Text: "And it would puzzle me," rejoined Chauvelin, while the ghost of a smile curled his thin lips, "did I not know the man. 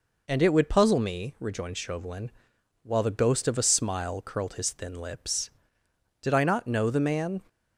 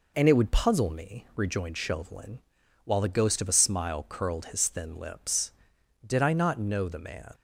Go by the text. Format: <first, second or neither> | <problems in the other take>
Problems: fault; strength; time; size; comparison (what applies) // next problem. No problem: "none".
neither | none